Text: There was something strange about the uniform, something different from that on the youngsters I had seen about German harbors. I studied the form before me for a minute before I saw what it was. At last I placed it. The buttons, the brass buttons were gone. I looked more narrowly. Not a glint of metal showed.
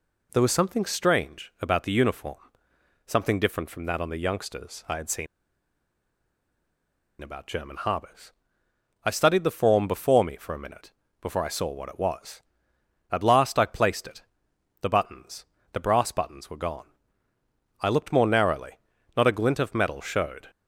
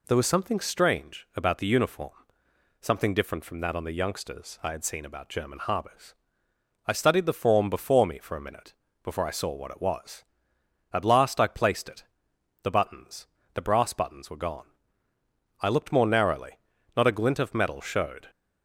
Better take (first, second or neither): second